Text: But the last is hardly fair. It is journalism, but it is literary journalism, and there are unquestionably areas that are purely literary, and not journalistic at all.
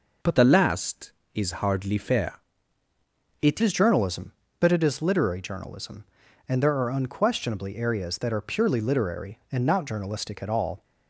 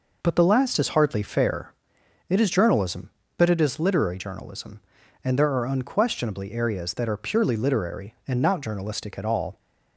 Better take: second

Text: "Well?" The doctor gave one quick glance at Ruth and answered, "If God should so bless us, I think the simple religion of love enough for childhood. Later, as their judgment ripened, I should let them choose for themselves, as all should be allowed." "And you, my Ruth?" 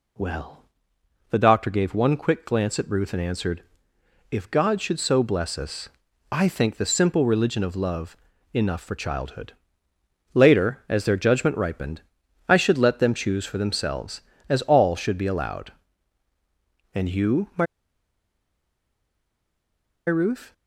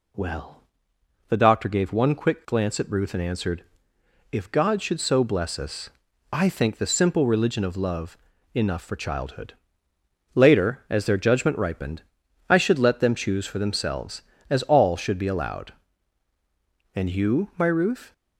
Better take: second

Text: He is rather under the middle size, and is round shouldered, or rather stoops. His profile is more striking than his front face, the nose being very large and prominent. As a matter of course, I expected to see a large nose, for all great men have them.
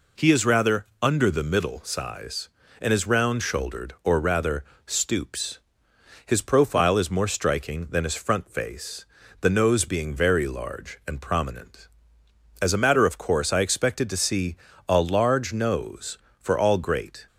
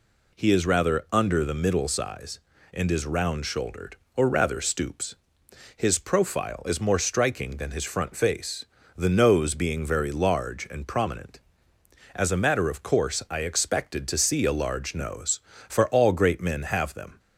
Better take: second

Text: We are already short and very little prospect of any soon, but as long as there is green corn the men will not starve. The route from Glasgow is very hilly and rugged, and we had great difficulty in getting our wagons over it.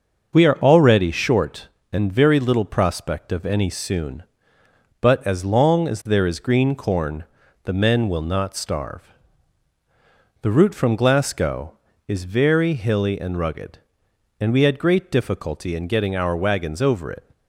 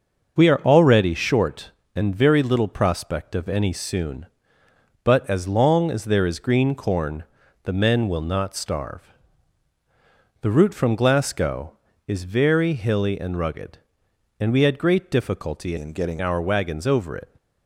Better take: first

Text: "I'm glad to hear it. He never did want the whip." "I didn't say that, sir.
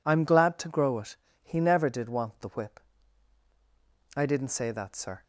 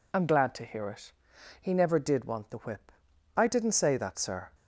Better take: second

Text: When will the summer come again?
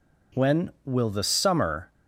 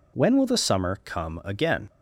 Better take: second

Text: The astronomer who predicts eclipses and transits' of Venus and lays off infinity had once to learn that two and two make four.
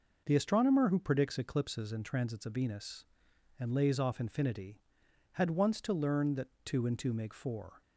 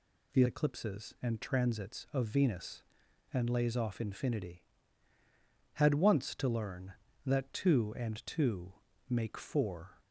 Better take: first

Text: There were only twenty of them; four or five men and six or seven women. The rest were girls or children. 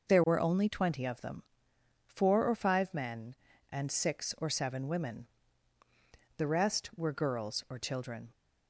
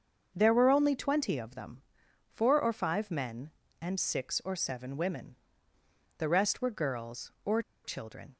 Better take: first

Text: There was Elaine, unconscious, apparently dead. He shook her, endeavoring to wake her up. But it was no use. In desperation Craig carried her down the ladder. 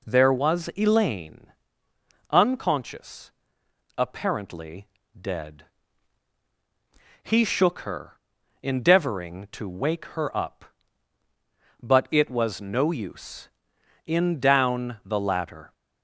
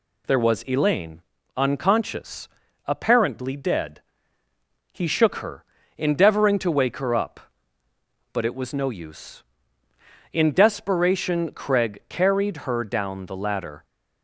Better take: second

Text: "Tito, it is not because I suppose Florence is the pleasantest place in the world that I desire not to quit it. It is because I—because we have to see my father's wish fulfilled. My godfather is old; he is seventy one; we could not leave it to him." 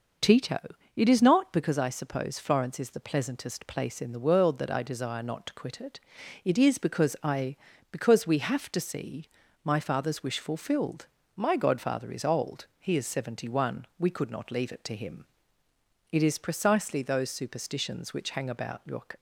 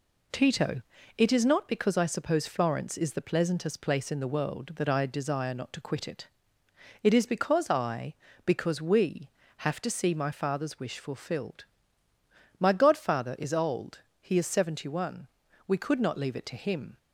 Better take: second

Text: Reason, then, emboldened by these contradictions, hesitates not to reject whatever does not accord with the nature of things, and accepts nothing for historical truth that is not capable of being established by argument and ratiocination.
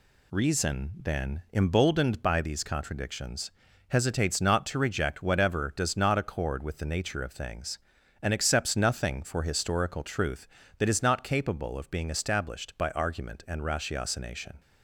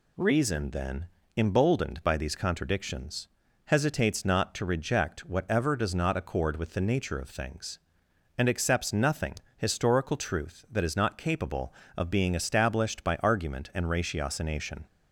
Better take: first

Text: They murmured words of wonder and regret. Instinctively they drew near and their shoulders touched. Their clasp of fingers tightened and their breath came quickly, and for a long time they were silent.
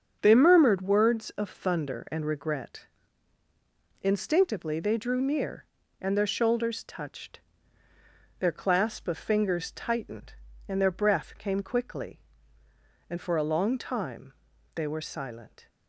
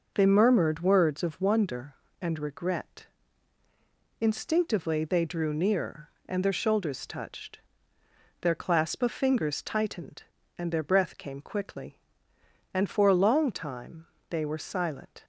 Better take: second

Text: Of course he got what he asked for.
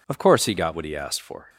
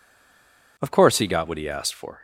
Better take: first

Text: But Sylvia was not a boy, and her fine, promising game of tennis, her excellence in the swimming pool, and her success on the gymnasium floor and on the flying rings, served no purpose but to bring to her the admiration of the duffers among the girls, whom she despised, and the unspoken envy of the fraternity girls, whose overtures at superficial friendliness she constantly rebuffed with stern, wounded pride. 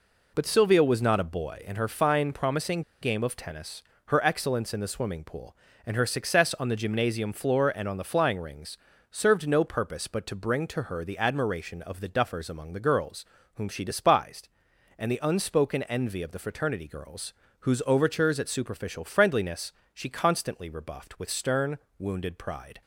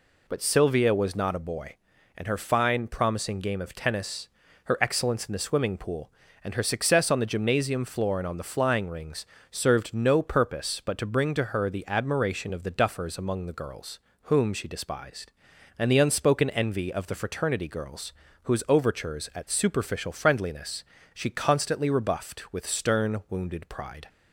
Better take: second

